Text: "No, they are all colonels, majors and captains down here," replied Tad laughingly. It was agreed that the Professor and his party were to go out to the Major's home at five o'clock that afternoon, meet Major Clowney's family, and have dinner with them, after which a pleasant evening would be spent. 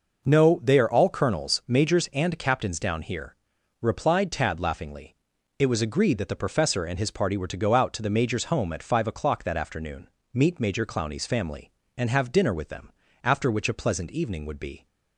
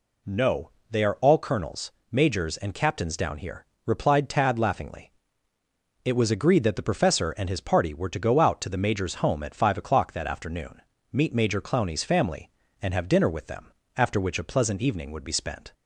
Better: second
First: stops before "spent"; at 14.8 s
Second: none

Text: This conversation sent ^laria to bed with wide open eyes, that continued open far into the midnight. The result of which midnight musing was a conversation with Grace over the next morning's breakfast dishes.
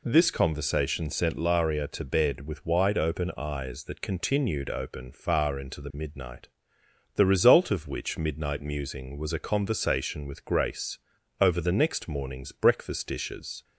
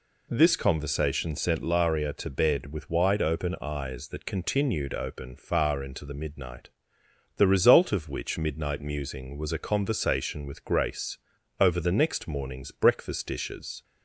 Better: neither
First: pauses between "Grace" and "over"; at 10.9 s; 0.42 s long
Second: pauses between "Grace" and "over"; at 11.1 s; 0.42 s long

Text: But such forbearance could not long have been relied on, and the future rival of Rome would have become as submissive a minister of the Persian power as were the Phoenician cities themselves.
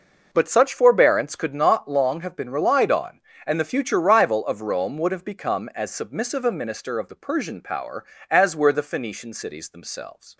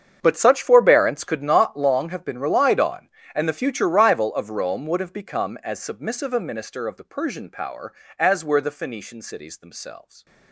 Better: first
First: none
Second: gets quieter; strong; throughout; 17 dB

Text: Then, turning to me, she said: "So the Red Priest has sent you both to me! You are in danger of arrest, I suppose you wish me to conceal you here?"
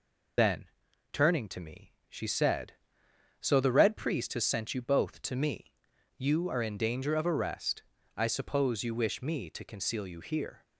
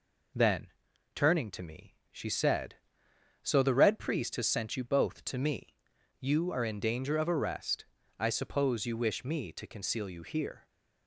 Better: second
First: loses the start of "Then"; at 0.3 s; 55 ms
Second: none

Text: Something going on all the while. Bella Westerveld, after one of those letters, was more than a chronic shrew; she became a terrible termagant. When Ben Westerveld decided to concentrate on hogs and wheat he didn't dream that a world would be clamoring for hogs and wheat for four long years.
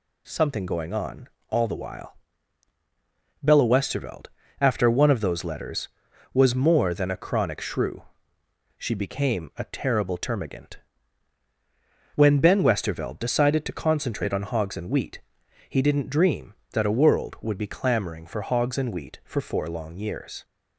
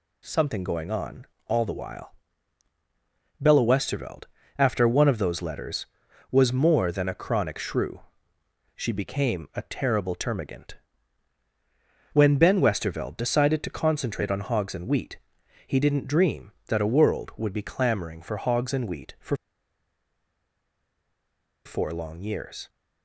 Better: first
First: pauses between "on" and "all"; slight; at 1.2 s; 0.22 s long // pauses between "wheat" and "he"; noticeable; at 15.2 s; 0.48 s long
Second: pauses between "on" and "all"; slight; at 1.2 s; 0.22 s long // pauses between "wheat" and "he"; noticeable; at 15.1 s; 0.48 s long // pauses between "for" and "four"; strong; at 19.3 s; 2.2 s long

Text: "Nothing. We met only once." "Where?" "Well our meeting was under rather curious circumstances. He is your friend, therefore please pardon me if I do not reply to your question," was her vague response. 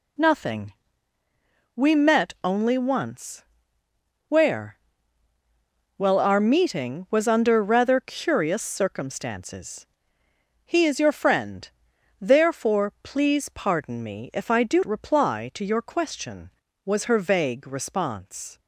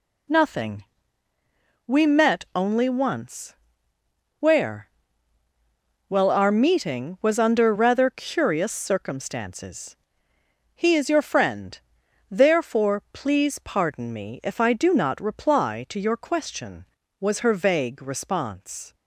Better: second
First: skips "not"; at 14.8 s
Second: none

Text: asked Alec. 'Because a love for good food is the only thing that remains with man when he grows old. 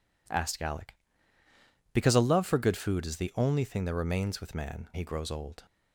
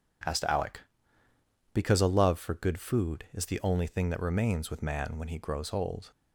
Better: second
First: skips "when"; at 4.9 s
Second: none

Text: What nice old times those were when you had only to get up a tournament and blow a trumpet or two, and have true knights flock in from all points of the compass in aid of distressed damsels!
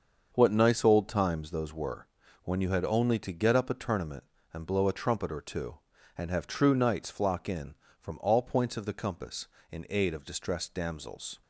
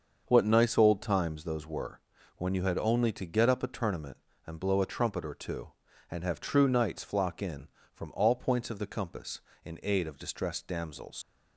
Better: first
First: starts louder than the rest; until 1.3 s; 6.5 dB // pauses between "were" and "when"; at 2.0 s; 0.38 s long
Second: starts louder than the rest; until 1.2 s; 6.5 dB // pauses between "were" and "when"; at 1.9 s; 0.38 s long // leaves "damsels" unfinished; at 11.2 s; 130 ms

